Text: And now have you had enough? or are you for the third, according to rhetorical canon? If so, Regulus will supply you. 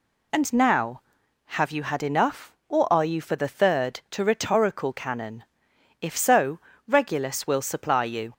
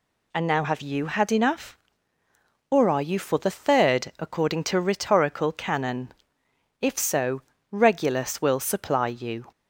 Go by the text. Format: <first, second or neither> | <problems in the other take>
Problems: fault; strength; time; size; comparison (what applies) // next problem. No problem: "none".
second | skips "according"; at 4.0 s